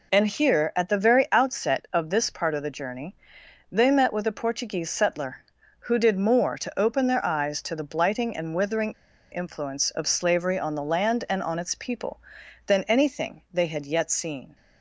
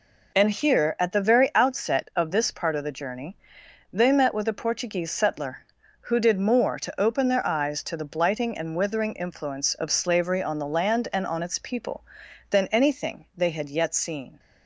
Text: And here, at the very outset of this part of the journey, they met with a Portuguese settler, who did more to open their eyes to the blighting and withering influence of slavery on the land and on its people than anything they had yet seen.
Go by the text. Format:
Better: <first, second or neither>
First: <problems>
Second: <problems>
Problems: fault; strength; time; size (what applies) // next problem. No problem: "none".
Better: second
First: pauses between "withering" and "influence"; at 8.9 s; 0.38 s long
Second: none